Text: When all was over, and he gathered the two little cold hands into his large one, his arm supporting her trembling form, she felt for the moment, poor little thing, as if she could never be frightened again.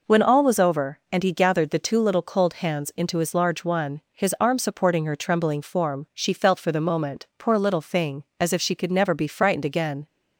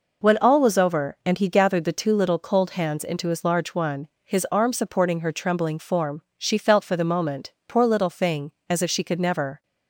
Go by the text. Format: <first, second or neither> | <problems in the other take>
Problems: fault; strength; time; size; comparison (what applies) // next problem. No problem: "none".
first | stops before "be frightened again"; at 9.6 s